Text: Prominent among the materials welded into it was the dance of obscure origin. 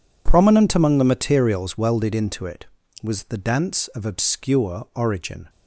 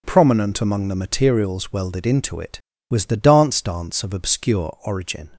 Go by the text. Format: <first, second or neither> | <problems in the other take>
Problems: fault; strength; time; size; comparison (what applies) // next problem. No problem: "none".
first | says "dance" twice; at 3.6 s